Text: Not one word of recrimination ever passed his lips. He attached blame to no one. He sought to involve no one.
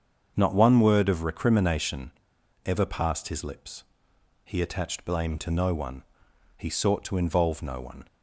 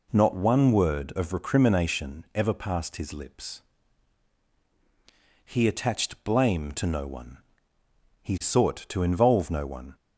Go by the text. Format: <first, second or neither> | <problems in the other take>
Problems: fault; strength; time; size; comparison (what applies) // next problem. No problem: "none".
second | starts louder than the rest; until 1.3 s; 7 dB // pauses between "recrimination" and "ever"; noticeable; at 2.0 s; 0.57 s long